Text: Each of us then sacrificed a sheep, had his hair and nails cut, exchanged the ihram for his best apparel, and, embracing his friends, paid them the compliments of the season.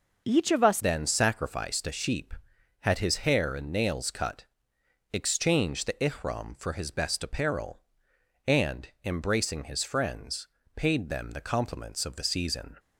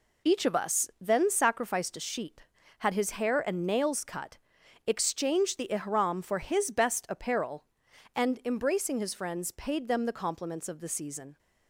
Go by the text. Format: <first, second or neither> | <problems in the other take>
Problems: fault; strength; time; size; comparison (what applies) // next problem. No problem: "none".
second | changes voice at "then"; from 0.7 s on; 12.0 s long